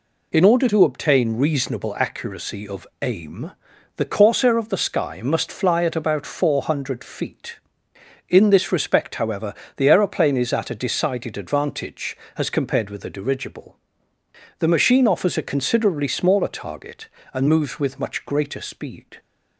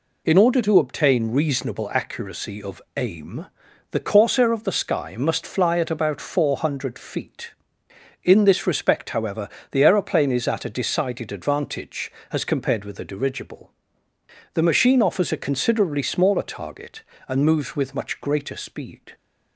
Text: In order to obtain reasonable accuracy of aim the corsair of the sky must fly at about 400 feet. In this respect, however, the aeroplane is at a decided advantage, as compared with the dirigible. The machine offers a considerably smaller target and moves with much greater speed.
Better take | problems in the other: neither | pauses between "aim" and "the"; the same in both

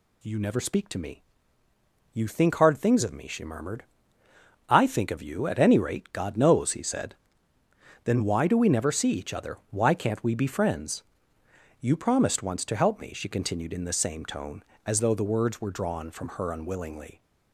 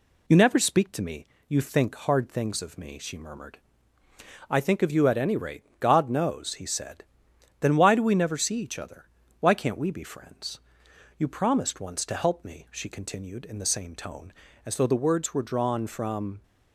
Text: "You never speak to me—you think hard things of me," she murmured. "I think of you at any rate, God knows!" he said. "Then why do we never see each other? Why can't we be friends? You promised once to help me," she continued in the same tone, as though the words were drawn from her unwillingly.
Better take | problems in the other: first | stops before "her unwillingly"; at 16.4 s

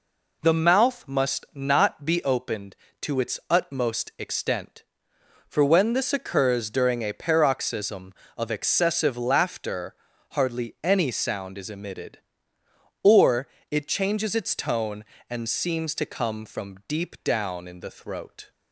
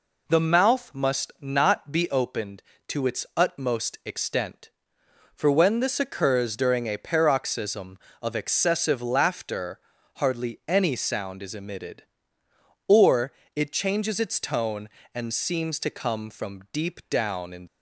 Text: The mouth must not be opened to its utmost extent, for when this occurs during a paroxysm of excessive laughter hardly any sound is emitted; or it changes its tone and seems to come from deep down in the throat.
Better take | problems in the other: first | pauses between "laughter" and "hardly"; slight; at 9.8 s; 0.36 s long; slight in the first // pauses between "or" and "it"; slight; at 13.3 s; 0.22 s long; slight in the first // stops before "the throat"; at 17.6 s

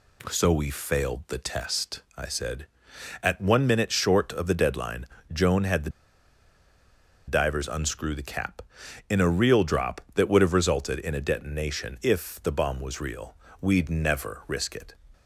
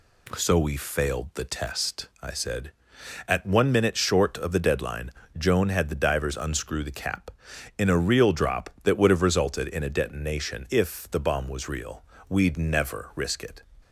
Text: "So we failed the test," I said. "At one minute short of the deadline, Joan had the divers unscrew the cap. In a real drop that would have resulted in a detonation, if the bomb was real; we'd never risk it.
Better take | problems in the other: second | pauses between "the" and "divers"; strong; at 5.8 s; 1.3 s long

